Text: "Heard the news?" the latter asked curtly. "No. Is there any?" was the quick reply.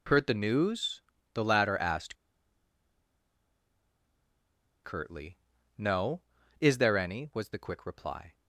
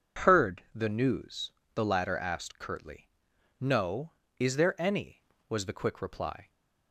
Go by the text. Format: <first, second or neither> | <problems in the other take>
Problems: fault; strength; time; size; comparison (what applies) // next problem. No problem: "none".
second | pauses between "asked" and "curtly"; strong; at 2.1 s; 2.6 s long